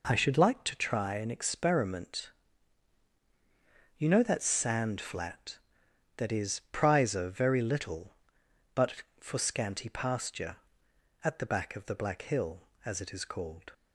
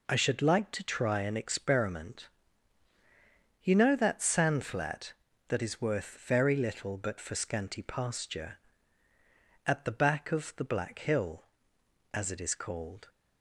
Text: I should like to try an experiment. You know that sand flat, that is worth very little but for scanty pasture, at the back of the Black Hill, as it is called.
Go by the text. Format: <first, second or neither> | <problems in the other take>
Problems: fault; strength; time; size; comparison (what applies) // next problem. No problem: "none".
second | says "prizer" for "worth"; at 6.7 s